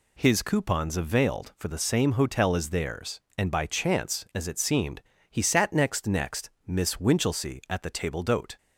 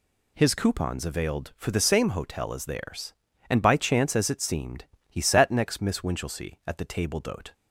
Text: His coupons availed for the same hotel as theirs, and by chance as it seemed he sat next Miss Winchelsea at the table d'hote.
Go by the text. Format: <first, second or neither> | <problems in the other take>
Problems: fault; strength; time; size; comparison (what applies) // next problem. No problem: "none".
second | pauses between "seemed" and "he"; slight; at 4.9 s; 0.30 s long; slight in the second // says "next" twice; at 6.0 s